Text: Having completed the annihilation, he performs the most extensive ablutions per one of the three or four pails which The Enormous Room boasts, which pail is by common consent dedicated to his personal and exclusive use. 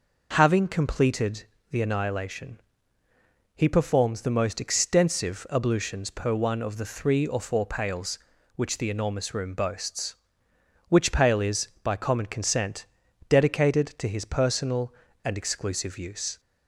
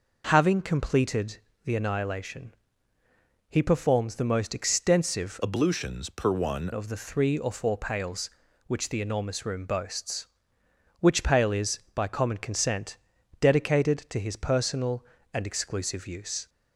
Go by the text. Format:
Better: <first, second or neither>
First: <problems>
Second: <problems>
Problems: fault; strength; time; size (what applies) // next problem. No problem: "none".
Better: first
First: pauses between "completed" and "the"; slight; at 1.4 s; 0.28 s long // pauses between "consent" and "dedicated"; at 12.8 s; 0.42 s long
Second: pauses between "completed" and "the"; slight; at 1.3 s; 0.28 s long // changes voice from "ablutions" to "one"; from 5.4 to 6.6 s; 1.2 s long // pauses between "consent" and "dedicated"; at 12.9 s; 0.42 s long